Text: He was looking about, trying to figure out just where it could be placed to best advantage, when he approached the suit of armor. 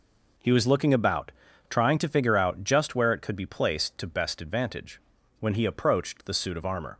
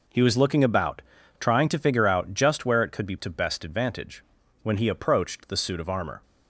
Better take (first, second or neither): first